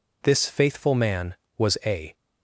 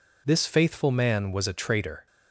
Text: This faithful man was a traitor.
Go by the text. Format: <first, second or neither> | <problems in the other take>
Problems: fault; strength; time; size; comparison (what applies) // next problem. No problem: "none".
second | stops before "traitor"; at 2.1 s